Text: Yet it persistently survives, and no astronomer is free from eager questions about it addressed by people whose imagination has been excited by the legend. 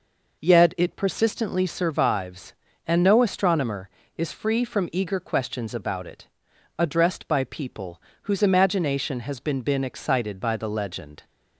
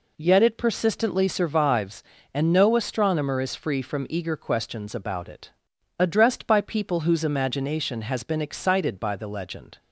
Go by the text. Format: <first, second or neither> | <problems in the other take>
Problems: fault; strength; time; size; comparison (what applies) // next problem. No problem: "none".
second | pauses between "it" and "addressed"; noticeable; at 6.2 s; 0.52 s long; noticeable in the second // pauses between "people" and "whose"; slight; at 8.0 s; 0.22 s long // says "been" twice; at 9.6 s